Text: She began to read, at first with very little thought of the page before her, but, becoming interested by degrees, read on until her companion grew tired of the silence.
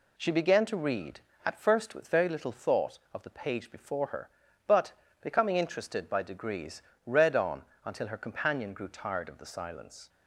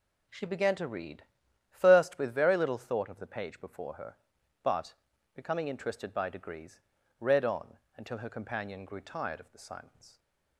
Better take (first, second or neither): first